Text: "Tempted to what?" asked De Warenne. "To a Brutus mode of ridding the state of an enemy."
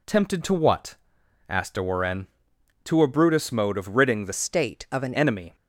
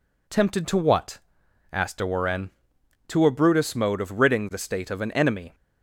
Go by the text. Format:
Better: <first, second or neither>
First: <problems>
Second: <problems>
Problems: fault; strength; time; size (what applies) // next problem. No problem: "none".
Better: second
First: changes voice from "state" to "an"; from 4.3 to 5.1 s; 0.8 s long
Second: none